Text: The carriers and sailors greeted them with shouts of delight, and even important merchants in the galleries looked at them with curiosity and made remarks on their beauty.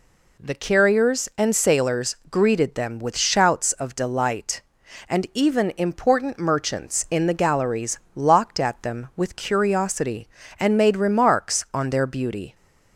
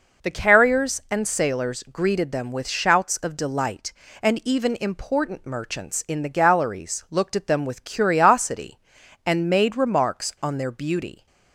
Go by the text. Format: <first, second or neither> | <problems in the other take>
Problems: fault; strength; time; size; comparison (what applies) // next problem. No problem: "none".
second | says "locked" for "looked"; at 8.1 s